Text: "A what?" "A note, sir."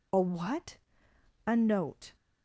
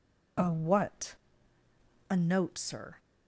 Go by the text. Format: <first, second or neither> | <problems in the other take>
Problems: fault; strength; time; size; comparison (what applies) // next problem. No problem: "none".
second | stops before "sir"; at 2.1 s